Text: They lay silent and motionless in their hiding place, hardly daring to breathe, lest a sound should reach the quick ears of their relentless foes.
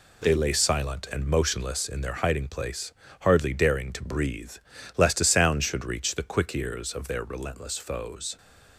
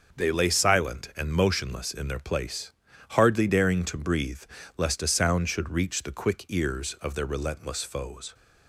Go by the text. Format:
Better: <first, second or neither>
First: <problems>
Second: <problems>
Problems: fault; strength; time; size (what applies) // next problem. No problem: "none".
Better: first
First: none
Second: starts louder than the rest; until 1.2 s; 6.5 dB // skips "hiding"; at 2.1 s